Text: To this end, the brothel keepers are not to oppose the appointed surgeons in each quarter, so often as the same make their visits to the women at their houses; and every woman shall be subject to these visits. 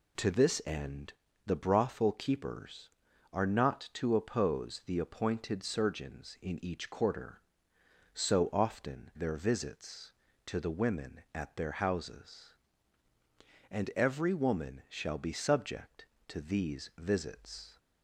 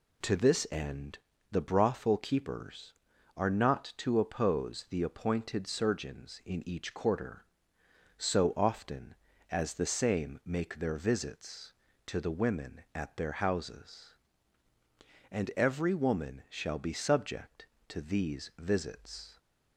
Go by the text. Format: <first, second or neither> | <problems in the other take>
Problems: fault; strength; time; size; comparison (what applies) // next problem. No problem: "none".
second | skips "as the same make"; at 9.1 s